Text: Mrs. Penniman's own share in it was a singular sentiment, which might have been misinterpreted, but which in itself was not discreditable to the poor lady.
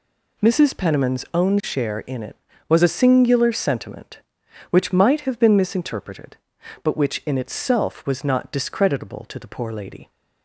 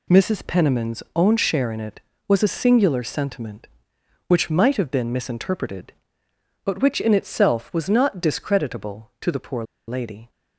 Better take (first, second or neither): first